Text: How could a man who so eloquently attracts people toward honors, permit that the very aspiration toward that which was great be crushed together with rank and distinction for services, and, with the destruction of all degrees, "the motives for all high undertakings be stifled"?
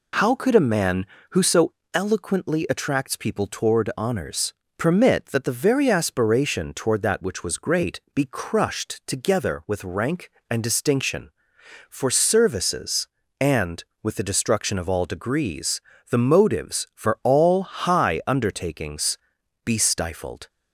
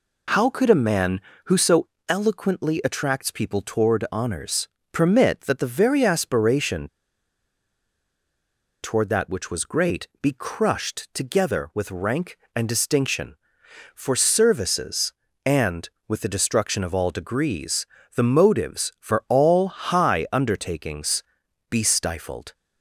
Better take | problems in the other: first | pauses between "so" and "eloquently"; slight; at 1.8 s; 0.20 s long; slight in the first // pauses between "aspiration" and "toward"; strong; at 6.8 s; 1.9 s long // pauses between "undertakings" and "be"; noticeable; at 21.2 s; 0.48 s long; noticeable in the first

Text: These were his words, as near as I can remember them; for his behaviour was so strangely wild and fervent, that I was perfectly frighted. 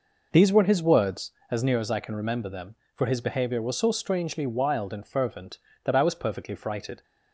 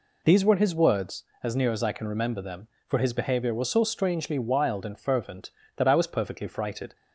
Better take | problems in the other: second | starts louder than the rest; noticeable; until 1.8 s; 5 dB

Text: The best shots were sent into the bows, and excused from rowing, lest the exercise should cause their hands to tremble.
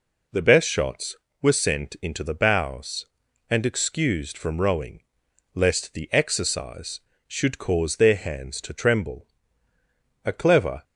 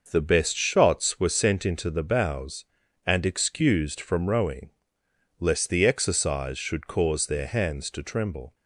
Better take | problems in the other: second | goes on to say "A clever"; from 10.2 s on; 0.60 s long

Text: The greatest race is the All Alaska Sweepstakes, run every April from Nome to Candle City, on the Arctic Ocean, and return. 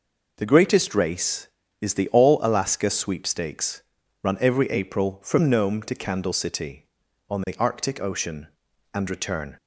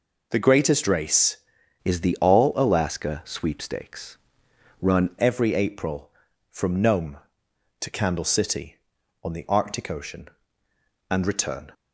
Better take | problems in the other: first | changes voice from "is" to "run"; from 1.8 to 5.0 s; 3.2 s long

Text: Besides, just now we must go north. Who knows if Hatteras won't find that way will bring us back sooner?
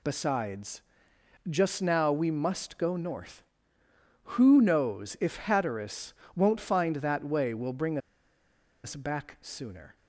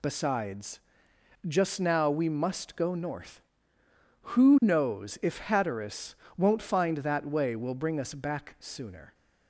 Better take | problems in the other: second | pauses between "Hatteras" and "won't"; slight; at 6.1 s; 0.22 s long; slight in the second // pauses between "bring" and "us"; noticeable; at 7.9 s; 0.85 s long

